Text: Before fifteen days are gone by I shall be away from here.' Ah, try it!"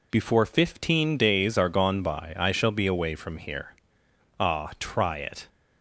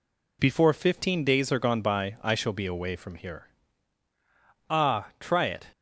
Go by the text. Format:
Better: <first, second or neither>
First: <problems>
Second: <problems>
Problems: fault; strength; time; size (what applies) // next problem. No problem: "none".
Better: neither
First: none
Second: none